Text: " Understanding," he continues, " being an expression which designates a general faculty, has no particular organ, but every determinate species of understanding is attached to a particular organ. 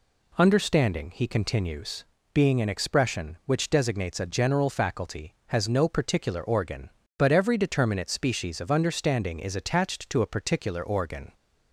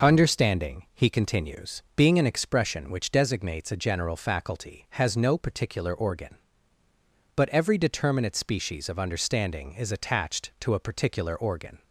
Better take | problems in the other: neither | none

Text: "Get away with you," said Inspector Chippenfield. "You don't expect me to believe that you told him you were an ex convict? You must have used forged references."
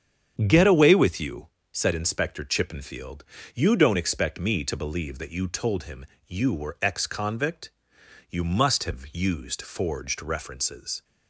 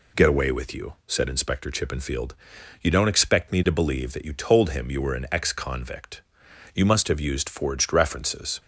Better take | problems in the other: second | starts louder than the rest; strong; until 1.4 s; 8 dB // pauses between "him" and "you"; slight; at 6.0 s; 0.22 s long // skips "an"; at 6.7 s

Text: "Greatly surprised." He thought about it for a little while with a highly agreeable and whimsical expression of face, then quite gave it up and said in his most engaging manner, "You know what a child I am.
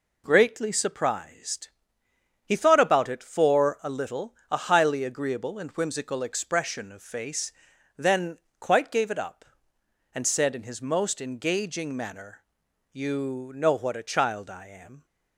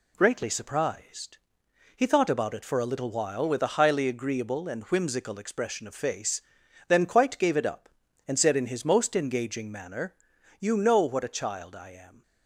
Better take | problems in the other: second | skips "while with"; at 4.4 s // pauses between "then" and "quite"; slight; at 8.3 s; 0.20 s long

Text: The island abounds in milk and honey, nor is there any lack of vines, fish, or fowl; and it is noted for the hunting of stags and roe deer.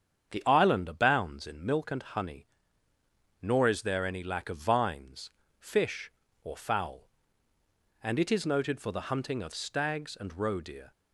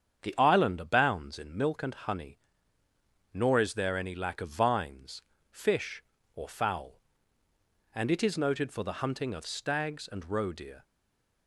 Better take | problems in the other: first | starts louder than the rest; strong; until 1.2 s; 8 dB; strong in the first // stays silent after the last word; slight; from 10.8 s on; 0.6 s long

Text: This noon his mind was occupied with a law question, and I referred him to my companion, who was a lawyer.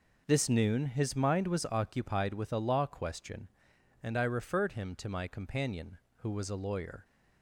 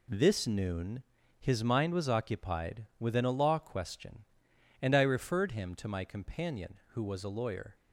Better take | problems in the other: first | pauses between "noon" and "his"; slight; at 1.0 s; 0.36 s long // says "within" for "with"; at 2.9 s

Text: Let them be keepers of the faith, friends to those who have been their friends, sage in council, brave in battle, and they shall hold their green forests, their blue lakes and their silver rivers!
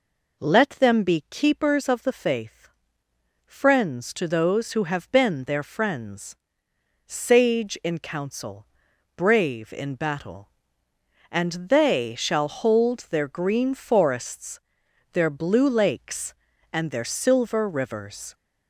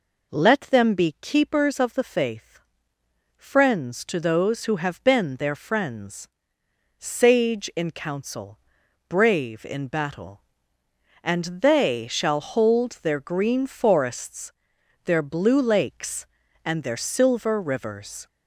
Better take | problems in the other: neither | none

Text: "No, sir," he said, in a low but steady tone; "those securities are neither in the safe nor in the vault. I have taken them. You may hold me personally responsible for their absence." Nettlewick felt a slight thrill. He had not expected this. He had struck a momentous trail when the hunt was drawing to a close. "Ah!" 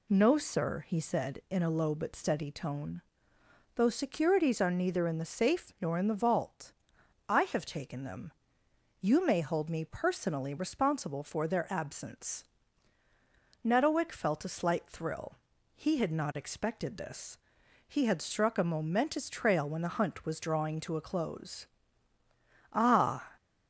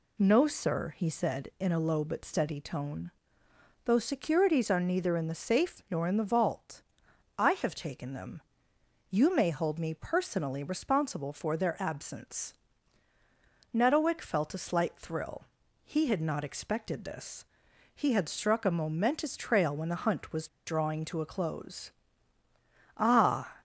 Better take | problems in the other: first | pauses between "was" and "drawing"; slight; at 20.4 s; 0.19 s long

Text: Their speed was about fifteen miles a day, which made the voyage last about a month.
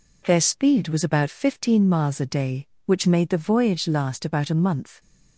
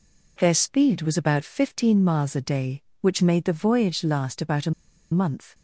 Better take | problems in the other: first | pauses between "a" and "month"; at 4.7 s; 0.41 s long

